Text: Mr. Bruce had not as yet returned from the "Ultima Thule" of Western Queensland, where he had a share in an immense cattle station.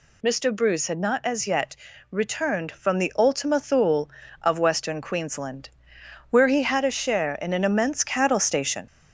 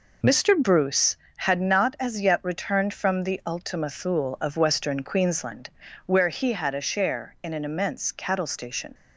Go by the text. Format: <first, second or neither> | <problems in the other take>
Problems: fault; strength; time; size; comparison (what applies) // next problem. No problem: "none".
second | gets louder; slight; throughout; 3 dB // pauses between "yet" and "returned"; slight; at 1.7 s; 0.36 s long